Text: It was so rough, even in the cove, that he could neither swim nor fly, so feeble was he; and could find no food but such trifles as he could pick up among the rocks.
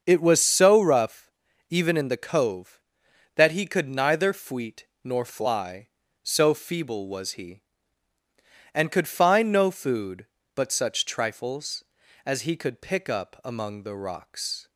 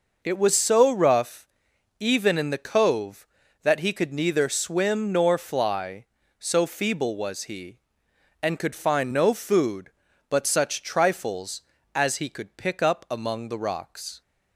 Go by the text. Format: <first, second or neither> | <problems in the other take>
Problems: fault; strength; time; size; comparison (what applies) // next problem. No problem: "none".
second | starts louder than the rest; until 1.0 s; 6.5 dB // says "fweet" for "swim"; at 4.3 s